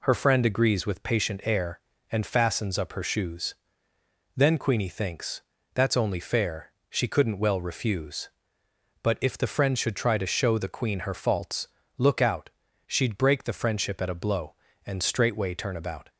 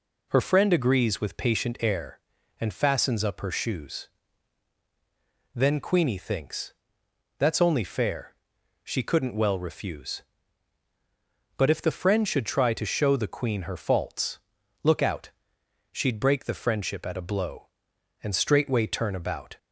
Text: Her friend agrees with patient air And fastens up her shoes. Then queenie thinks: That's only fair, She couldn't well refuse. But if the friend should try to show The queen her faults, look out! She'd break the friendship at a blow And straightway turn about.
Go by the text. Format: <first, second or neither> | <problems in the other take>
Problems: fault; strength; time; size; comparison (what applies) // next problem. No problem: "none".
neither | none